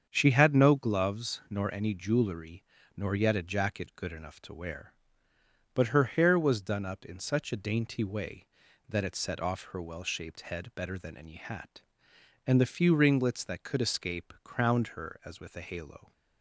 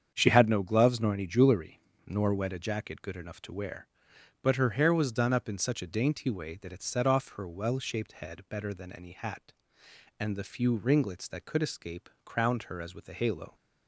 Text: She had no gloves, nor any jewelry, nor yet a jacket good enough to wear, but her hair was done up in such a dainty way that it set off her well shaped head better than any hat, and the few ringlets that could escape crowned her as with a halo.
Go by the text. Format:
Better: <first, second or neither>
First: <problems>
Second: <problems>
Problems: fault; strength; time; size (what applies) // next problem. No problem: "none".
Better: first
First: starts louder than the rest; strong; until 1.1 s; 7.5 dB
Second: starts louder than the rest; strong; until 1.1 s; 7.5 dB // says "wet" for "yet"; at 2.3 s // pauses between "escape" and "crowned"; slight; at 12.0 s; 0.16 s long